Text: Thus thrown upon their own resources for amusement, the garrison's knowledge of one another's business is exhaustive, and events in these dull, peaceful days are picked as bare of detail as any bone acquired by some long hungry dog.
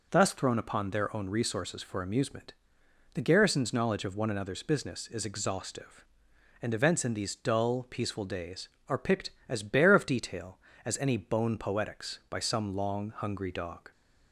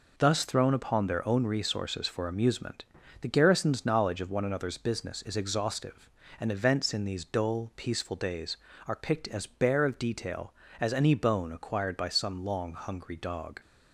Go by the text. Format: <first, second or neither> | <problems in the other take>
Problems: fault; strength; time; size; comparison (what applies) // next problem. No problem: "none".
second | says "poetics" for "acquired"; at 11.5 s